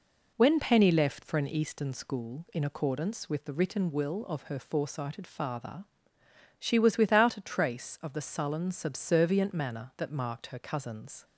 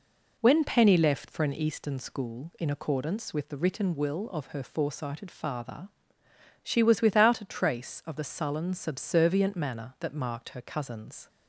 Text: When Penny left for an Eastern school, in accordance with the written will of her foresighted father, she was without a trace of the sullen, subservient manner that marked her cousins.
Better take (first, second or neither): neither